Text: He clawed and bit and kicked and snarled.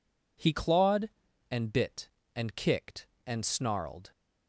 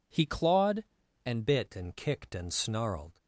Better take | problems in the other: first | changes voice at "bit"; from 1.4 s on; 1.7 s long

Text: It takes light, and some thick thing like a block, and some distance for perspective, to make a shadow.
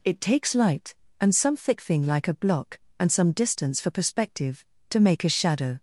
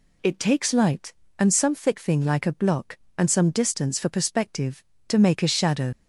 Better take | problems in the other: first | leaves "shadow" unfinished; at 5.9 s; 65 ms

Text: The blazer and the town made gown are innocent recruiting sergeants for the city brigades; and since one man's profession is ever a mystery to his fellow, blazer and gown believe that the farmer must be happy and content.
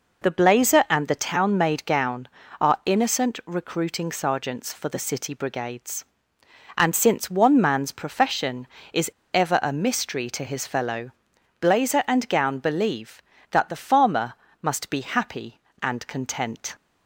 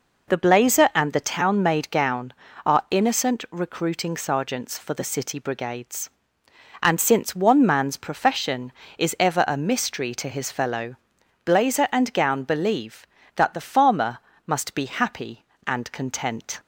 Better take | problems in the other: second | pauses between "is" and "ever"; slight; at 9.1 s; 0.22 s long // pauses between "farmer" and "must"; slight; at 14.3 s; 0.28 s long; slight in the second

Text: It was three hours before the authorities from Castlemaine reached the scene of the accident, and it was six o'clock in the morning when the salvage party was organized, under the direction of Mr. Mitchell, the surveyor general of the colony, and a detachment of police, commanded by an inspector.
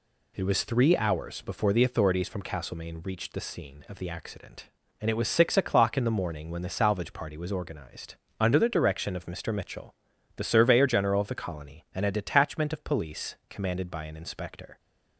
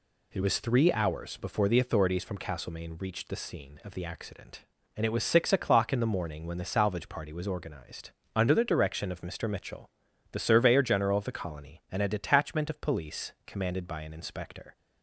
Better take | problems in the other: neither | none

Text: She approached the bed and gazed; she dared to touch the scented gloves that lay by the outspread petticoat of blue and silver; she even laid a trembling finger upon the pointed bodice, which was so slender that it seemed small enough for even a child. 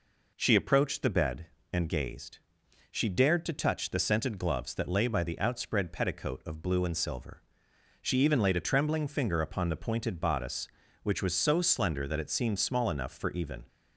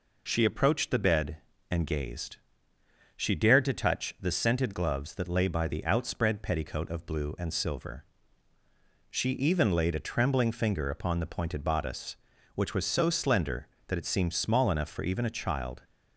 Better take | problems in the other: second | stops before "a child"; at 13.6 s

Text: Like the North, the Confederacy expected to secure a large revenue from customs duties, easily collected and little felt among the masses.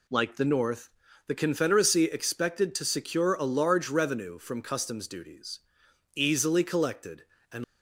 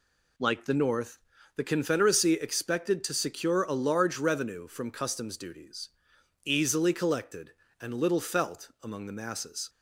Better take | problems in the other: second | stops before "little felt among the masses"; at 7.6 s

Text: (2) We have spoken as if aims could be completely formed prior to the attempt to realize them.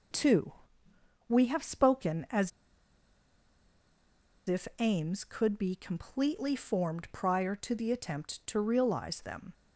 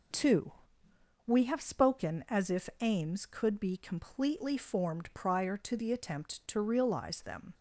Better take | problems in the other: second | pauses between "as" and "if"; strong; at 2.5 s; 1.9 s long

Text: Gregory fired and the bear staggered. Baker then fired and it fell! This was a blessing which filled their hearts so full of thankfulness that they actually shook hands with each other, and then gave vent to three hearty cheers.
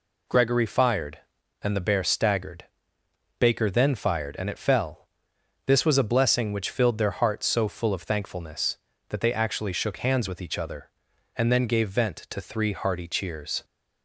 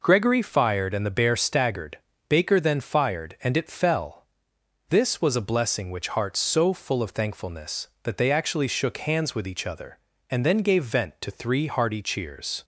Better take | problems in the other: first | skips "filled their"; at 6.0 s

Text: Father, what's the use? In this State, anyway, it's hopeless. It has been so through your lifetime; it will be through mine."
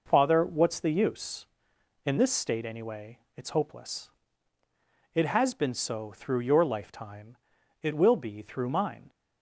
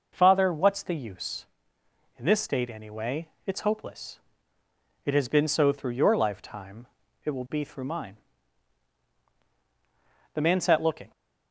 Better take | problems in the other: first | goes on to say "The man sat looking"; from 9.7 s on; 1.3 s long

